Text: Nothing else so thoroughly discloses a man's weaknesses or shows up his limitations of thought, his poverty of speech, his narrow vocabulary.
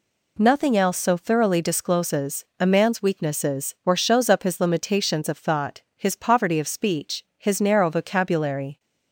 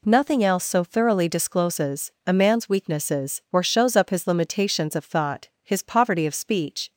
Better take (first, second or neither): first